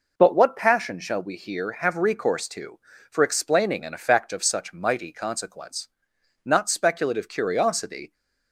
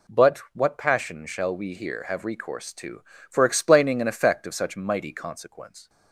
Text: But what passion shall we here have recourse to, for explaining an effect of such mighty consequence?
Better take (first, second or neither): second